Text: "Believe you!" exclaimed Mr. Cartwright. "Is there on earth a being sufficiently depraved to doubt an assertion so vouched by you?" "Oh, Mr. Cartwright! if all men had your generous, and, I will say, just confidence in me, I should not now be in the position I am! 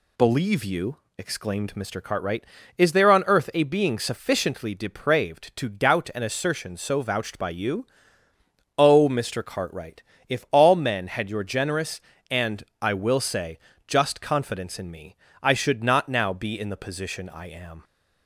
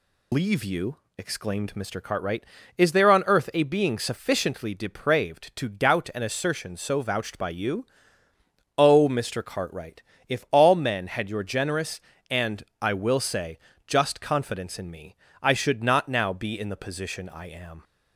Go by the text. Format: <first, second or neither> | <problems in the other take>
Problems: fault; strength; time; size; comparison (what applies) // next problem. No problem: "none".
first | loses the start of "Believe"; at 0.3 s; 145 ms